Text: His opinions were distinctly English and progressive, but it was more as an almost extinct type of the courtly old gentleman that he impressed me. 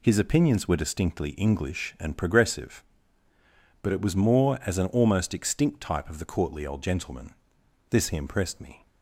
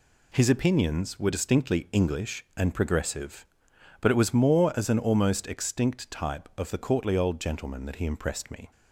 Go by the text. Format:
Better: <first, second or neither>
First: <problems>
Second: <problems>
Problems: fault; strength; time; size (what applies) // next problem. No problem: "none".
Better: second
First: says "this" for "that"; at 7.8 s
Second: none